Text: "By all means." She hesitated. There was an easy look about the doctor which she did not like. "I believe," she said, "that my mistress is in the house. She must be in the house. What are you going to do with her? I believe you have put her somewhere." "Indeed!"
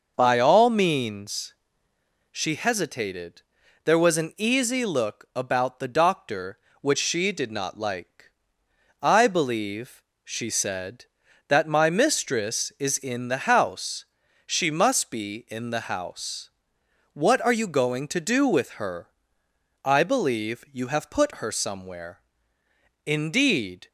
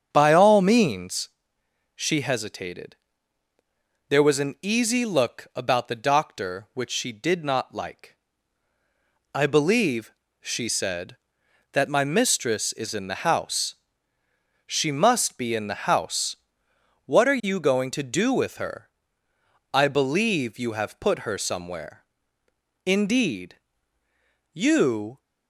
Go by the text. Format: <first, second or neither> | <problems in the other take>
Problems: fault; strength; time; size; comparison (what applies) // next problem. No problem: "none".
first | starts louder than the rest; strong; until 1.1 s; 7.5 dB // goes on to say "You"; noticeable; from 24.5 s on; 0.68 s long